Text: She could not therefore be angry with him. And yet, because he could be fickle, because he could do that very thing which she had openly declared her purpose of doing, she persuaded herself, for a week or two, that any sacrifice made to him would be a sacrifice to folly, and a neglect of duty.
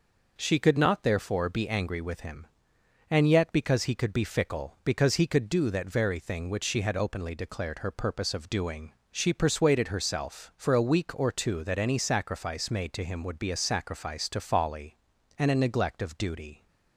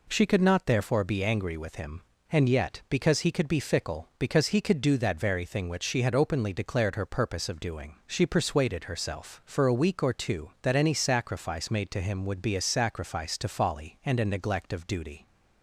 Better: neither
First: none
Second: none

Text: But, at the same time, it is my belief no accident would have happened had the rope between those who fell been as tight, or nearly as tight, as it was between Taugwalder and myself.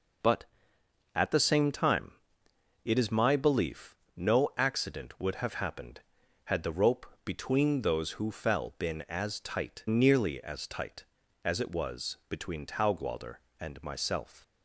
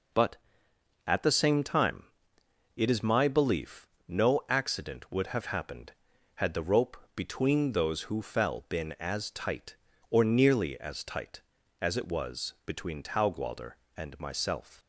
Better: second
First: pauses between "belief" and "no"; slight; at 3.9 s; 0.20 s long // pauses between "rope" and "between"; slight; at 7.0 s; 0.18 s long // skips "or"; at 9.8 s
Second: pauses between "belief" and "no"; slight; at 3.8 s; 0.20 s long // pauses between "rope" and "between"; slight; at 6.9 s; 0.18 s long

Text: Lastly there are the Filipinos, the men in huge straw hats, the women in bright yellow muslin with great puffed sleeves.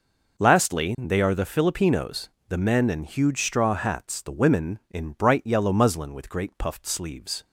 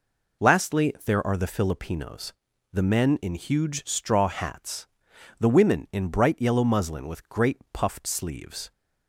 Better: second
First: says "they" for "there"; at 0.9 s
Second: none

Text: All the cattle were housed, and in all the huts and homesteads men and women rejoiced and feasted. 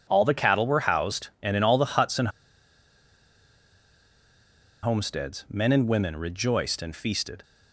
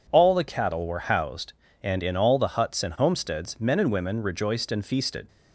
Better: second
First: pauses between "and" and "homesteads"; strong; at 2.2 s; 2.5 s long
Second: none

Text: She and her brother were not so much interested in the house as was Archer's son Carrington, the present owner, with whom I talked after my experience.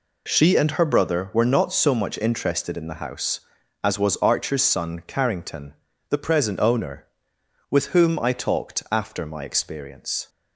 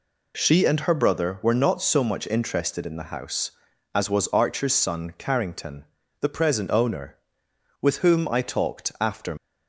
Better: first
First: none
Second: stops before "my experience"; at 9.3 s

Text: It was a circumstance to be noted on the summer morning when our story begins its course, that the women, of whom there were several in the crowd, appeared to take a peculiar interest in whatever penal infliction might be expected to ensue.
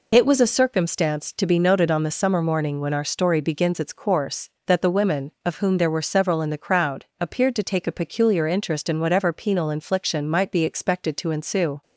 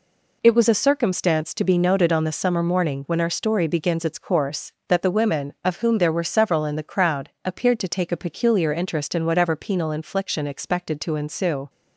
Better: first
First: none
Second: skips "might be"; at 10.4 s

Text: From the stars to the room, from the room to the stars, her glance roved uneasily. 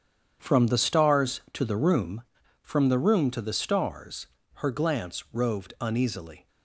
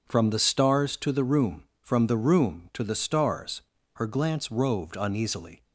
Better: neither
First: starts louder than the rest; strong; until 1.4 s; 8 dB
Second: starts louder than the rest; strong; until 1.1 s; 7 dB

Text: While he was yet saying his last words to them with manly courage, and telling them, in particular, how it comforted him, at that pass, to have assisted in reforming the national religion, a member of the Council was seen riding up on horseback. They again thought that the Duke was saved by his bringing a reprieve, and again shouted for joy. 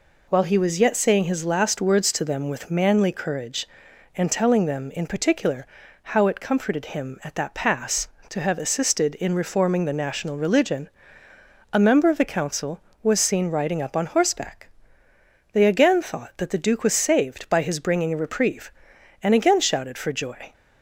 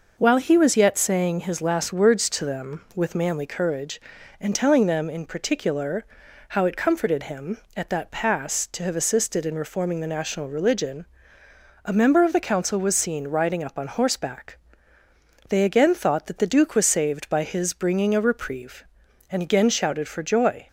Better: neither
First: none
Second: none

